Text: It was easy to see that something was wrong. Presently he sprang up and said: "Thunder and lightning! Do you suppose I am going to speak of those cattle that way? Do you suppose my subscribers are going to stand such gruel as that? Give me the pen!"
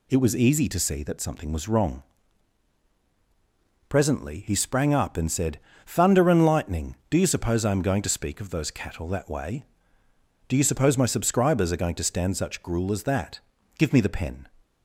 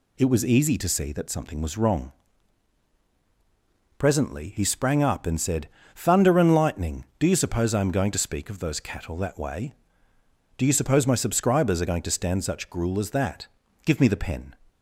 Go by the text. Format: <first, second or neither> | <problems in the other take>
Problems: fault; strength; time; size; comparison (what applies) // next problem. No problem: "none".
neither | none